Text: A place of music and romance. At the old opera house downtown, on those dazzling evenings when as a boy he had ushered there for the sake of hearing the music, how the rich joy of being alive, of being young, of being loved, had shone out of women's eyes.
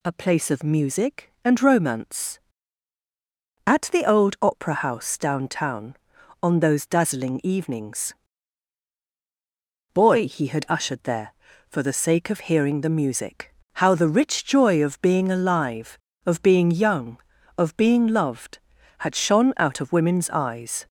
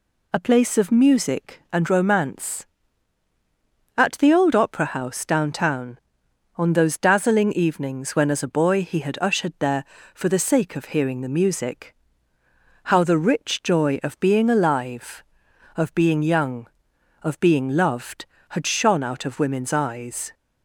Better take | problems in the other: second | skips "when as a"; at 9.0 s

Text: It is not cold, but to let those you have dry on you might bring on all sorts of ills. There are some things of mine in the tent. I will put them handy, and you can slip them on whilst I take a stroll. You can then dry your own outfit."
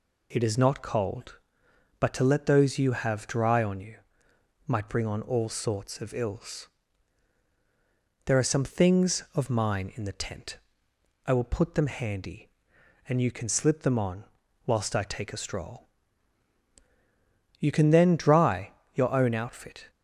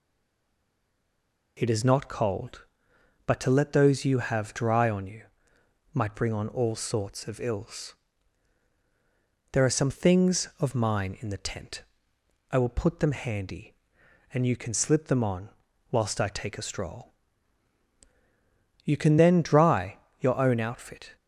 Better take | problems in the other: first | stays silent before the first word; noticeable; until 1.5 s; 1.5 s long // pauses between "you" and "might"; noticeable; at 5.2 s; 0.70 s long; noticeable in the first // pauses between "on" and "whilst"; at 15.4 s; 0.42 s long; also in the first // pauses between "dry" and "your"; slight; at 19.9 s; 0.22 s long; slight in the first

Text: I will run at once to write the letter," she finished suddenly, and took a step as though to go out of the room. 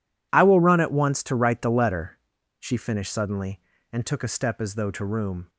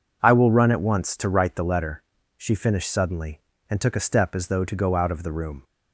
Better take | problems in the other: second | skips "go out of the"; at 5.0 s

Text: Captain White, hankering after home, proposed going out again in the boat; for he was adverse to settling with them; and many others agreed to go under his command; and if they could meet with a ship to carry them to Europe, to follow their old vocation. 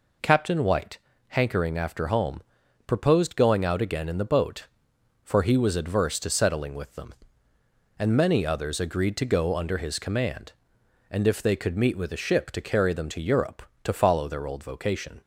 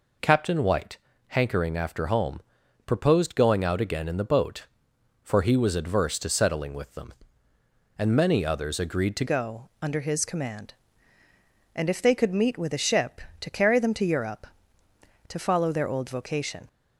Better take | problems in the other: first | changes voice at "go"; from 9.2 s on; 7.4 s long

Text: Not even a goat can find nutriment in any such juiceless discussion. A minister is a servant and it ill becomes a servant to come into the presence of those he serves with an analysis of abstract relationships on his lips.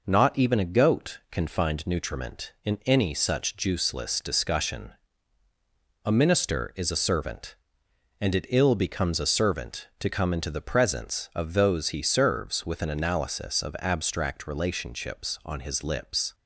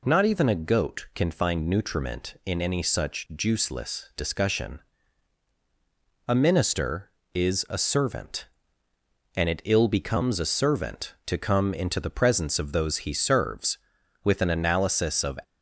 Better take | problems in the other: first | stops before "abstract relationships on his lips"; at 15.4 s

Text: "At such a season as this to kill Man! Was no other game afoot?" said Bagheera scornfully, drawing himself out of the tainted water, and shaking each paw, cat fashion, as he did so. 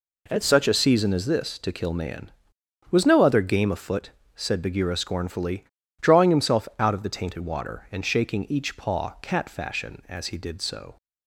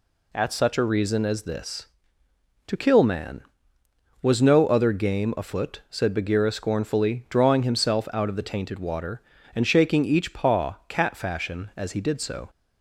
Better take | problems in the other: first | says "reason" for "season"; at 0.8 s

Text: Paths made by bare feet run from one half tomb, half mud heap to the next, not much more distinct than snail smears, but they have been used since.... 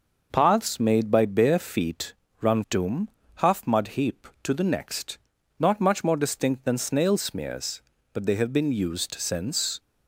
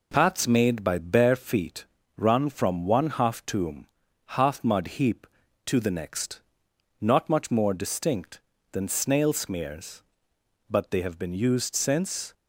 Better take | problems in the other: second | pauses between "feet" and "run"; slight; at 2.1 s; 0.26 s long; slight in the second // skips "from one half"; at 2.6 s

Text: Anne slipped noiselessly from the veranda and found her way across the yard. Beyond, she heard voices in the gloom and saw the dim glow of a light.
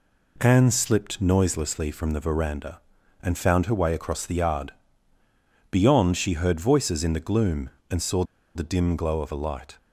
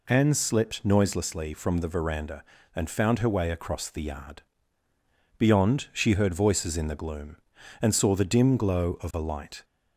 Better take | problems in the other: second | pauses between "saw" and "the"; slight; at 8.2 s; 0.32 s long

